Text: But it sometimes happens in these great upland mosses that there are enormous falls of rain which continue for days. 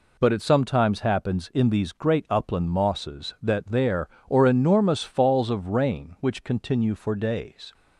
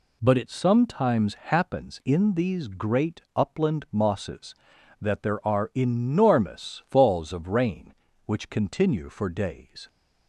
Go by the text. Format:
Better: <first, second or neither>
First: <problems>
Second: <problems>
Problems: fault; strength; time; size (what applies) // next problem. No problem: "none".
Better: second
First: says "or" for "are"; at 4.2 s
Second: none